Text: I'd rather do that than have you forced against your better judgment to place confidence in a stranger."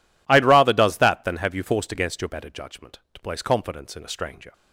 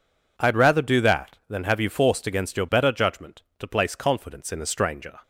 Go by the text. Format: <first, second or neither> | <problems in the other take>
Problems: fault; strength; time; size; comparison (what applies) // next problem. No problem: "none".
second | says "does" for "do"; at 0.7 s